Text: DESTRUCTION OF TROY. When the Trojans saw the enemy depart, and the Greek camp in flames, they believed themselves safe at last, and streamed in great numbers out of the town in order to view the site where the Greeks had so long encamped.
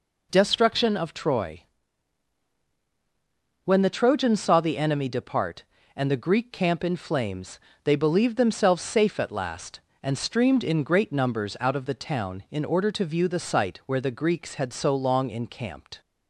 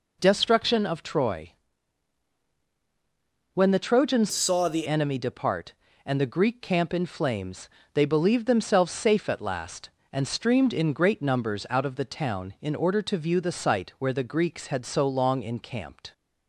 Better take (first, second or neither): first